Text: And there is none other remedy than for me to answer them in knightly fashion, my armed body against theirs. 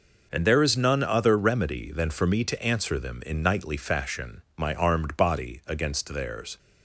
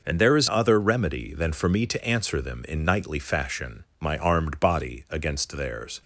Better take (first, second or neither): first